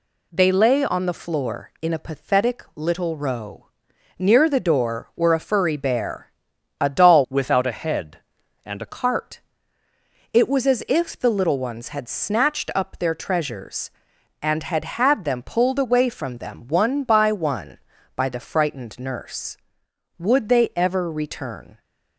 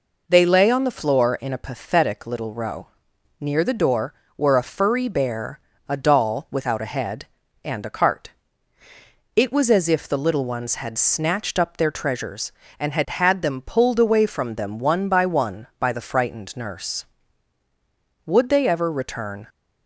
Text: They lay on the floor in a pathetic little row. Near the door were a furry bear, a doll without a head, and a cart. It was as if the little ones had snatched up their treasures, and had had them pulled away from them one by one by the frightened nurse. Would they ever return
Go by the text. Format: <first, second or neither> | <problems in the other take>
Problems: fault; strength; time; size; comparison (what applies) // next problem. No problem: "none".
second | changes voice from "without" to "a"; from 7.2 to 8.8 s; 1.6 s long